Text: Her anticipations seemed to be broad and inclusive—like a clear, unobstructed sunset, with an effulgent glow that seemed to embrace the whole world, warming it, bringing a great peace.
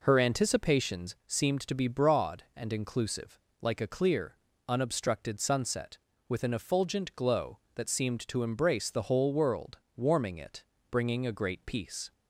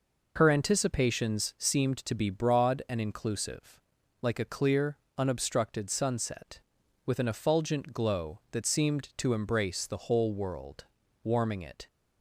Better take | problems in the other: first | stops before "bringing a great peace"; at 11.8 s

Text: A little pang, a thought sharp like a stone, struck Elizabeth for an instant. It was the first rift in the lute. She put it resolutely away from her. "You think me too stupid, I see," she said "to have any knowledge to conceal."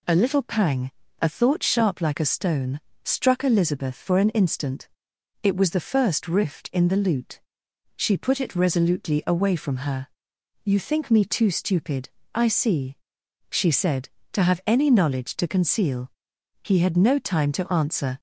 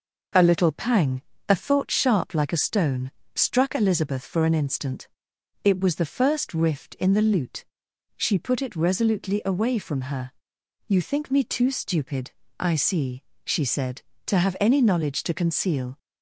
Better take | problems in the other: second | goes on to say "He had no time to answer"; from 16.6 s on; 1.5 s long

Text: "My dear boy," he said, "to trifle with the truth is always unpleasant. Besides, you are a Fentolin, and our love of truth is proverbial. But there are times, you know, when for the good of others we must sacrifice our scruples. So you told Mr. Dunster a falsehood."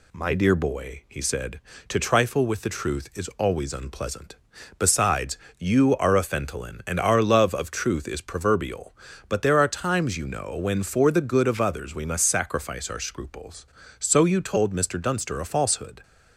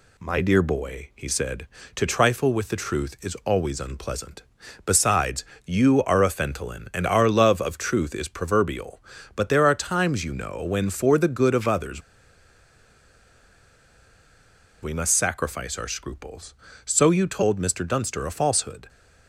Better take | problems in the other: first | pauses between "others" and "we"; strong; at 12.0 s; 2.8 s long

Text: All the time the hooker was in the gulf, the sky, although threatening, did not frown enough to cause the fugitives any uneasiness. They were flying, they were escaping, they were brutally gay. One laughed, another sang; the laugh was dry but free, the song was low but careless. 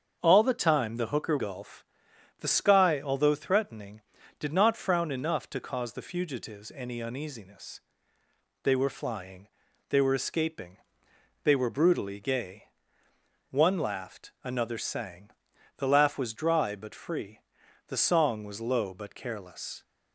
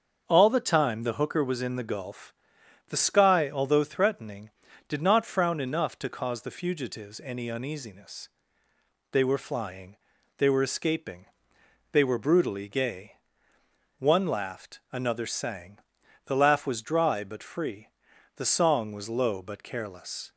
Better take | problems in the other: second | starts louder than the rest; until 1.2 s; 7 dB; also in the second // skips "was in the"; at 1.3 s

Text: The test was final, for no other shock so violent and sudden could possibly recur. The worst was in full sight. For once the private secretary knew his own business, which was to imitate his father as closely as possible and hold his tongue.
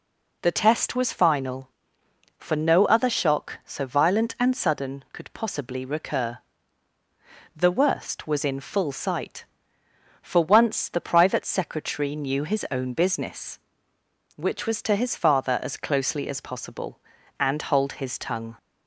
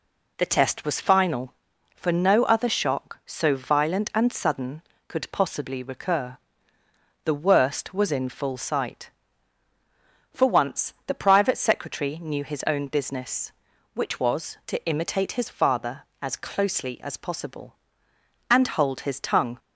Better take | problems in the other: second | skips "imitate"; at 14.9 s

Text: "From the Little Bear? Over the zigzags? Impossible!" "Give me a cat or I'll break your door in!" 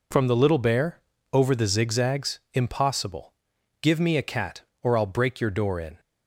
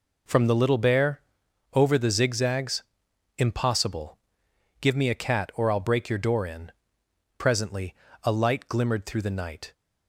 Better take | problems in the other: first | goes on to say "Presently a light glimmered through the night"; strong; from 7.3 s on; 2.3 s long

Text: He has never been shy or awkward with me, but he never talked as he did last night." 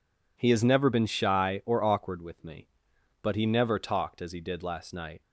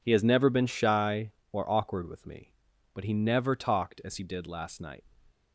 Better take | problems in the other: neither | none

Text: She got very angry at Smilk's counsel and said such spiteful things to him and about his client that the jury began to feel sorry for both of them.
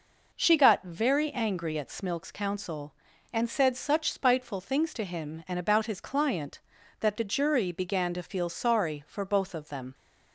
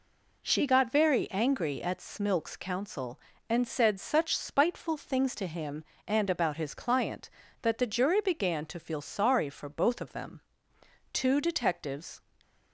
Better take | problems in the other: first | goes on to say "Two detectives"; noticeable; from 11.1 s on; 1.1 s long

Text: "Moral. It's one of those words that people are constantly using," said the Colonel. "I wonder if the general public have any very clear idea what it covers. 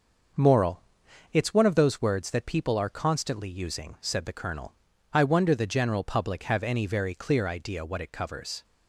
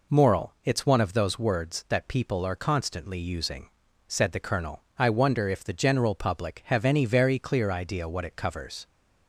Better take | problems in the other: second | starts louder than the rest; until 1.8 s; 6.5 dB // skips "if"; at 5.5 s

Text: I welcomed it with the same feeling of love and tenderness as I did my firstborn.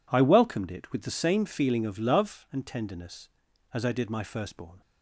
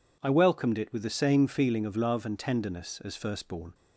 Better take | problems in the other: first | skips "I did my"; at 3.1 s

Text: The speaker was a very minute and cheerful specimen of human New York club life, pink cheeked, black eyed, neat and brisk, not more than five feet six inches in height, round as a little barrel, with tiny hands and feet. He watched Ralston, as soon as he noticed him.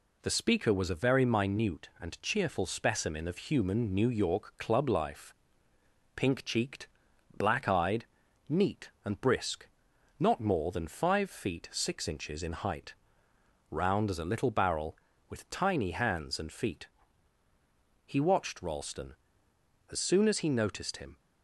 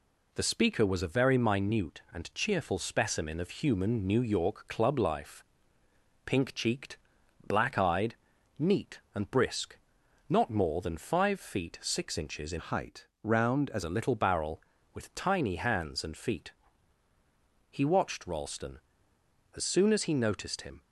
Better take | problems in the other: first | changes voice from "height" to "as"; from 12.5 to 13.8 s; 1.3 s long

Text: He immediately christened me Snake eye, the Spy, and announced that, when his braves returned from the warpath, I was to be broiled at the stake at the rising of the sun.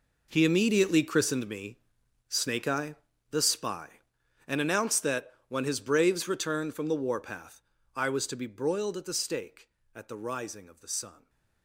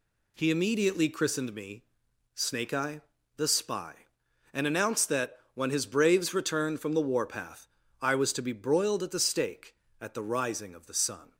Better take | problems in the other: second | gets quieter; strong; throughout; 15 dB // pauses between "me" and "Snake"; noticeable; at 1.7 s; 0.52 s long; noticeable in the second

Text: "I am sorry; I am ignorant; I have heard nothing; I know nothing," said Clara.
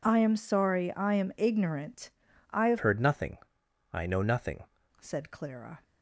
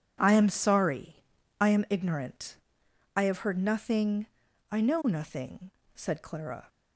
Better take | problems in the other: second | changes voice from "heard" to "nothing"; from 2.8 to 4.6 s; 1.8 s long

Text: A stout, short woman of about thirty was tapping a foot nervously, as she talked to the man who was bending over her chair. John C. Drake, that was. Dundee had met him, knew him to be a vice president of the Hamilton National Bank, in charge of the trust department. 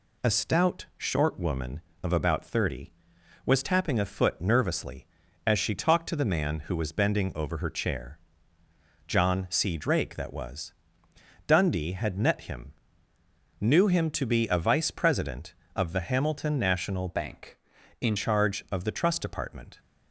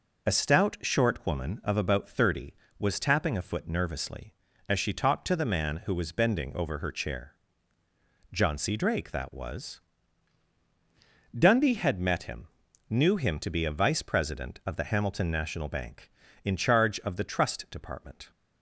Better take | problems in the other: second | changes voice from "Bank" to "in"; from 17.0 to 18.1 s; 1.1 s long

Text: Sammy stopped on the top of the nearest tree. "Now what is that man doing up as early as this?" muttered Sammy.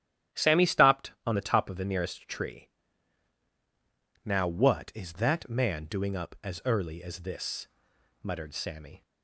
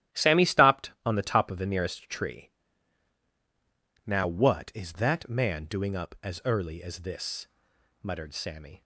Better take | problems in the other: first | gets quieter; strong; throughout; 10.5 dB // starts louder than the rest; strong; until 1.2 s; 12 dB; strong in the first

